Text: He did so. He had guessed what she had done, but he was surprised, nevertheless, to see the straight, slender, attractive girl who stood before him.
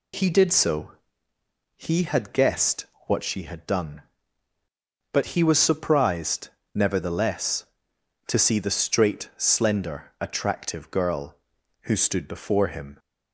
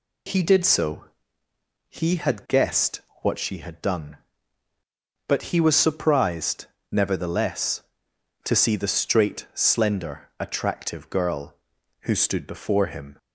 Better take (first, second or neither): neither